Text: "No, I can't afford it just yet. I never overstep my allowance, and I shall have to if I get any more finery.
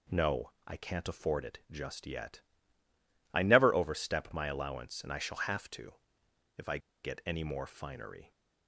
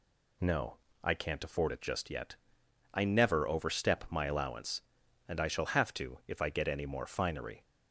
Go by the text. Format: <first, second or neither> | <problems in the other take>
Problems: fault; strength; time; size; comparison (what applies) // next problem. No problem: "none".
second | pauses between "to" and "if"; noticeable; at 5.9 s; 0.60 s long // pauses between "I" and "get"; slight; at 6.7 s; 0.25 s long